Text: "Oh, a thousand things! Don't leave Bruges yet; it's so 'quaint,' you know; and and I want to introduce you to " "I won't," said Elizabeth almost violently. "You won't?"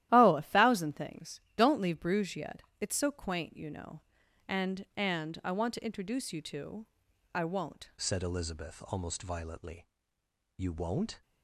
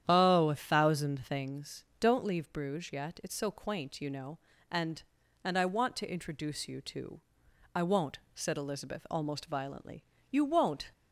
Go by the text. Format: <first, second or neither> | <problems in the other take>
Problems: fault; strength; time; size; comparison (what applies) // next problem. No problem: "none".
second | starts louder than the rest; strong; until 1.1 s; 13.5 dB; strong in the second // changes voice at "said"; from 7.9 s on; 3.3 s long